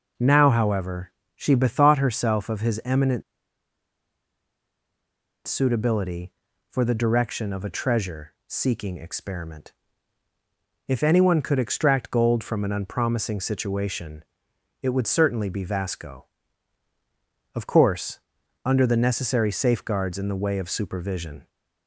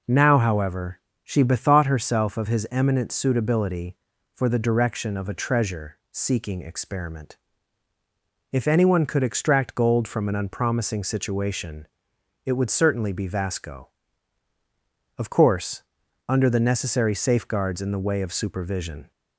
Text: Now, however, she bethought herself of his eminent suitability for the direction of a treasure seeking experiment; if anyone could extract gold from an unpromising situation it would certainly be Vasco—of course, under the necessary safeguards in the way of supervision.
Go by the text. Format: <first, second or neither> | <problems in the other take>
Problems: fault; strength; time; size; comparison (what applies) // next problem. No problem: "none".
second | pauses between "eminent" and "suitability"; strong; at 3.2 s; 2.2 s long // pauses between "situation" and "it"; noticeable; at 14.2 s; 0.60 s long; noticeable in the second